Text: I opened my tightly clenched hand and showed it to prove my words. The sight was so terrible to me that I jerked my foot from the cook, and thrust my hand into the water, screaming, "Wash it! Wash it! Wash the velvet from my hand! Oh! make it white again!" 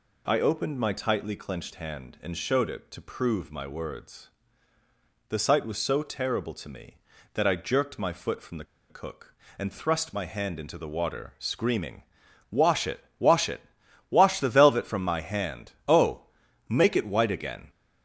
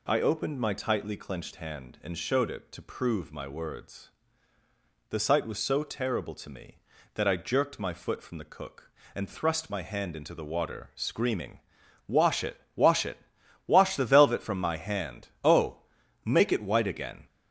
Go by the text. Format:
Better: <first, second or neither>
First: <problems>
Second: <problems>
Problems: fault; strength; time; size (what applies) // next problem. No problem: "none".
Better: second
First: pauses between "the" and "cook"; slight; at 8.6 s; 0.25 s long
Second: none